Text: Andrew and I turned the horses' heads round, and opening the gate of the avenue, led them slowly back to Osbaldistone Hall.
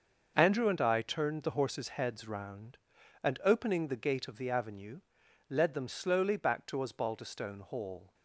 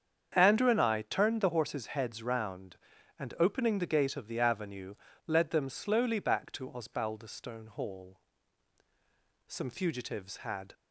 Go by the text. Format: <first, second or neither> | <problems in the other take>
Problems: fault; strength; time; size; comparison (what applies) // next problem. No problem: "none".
first | starts louder than the rest; strong; until 1.3 s; 7.5 dB; also in the first // goes on to say "Some fugitives had"; noticeable; from 9.4 s on; 1.2 s long